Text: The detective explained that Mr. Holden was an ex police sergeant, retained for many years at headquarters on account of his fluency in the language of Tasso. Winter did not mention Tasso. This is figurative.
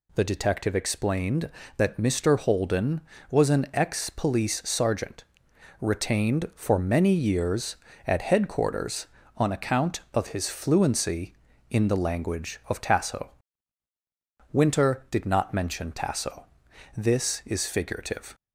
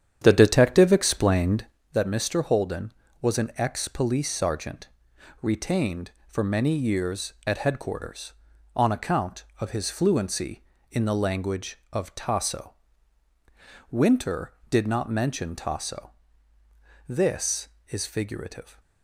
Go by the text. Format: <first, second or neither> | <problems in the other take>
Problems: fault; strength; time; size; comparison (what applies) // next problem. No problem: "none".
first | starts louder than the rest; strong; until 1.9 s; 9 dB